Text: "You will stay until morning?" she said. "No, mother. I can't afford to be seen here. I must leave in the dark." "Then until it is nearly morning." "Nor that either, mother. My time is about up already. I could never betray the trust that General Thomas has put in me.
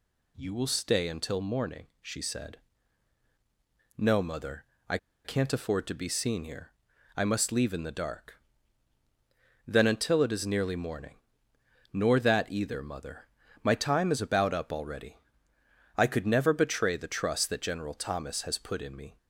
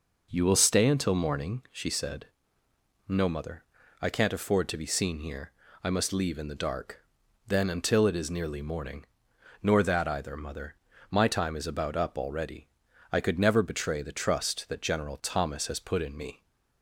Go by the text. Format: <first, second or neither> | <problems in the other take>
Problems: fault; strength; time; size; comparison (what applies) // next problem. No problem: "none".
second | pauses between "I" and "can't"; slight; at 4.9 s; 0.27 s long